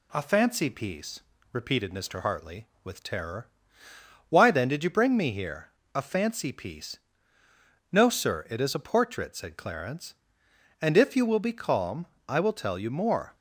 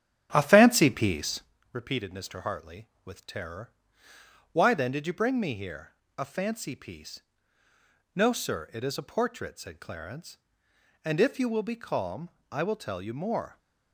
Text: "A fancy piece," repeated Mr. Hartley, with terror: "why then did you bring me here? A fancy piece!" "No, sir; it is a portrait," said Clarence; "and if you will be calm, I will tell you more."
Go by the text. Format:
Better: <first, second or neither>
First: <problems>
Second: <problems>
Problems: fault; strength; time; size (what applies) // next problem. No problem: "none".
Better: first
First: none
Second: starts louder than the rest; strong; until 1.5 s; 11 dB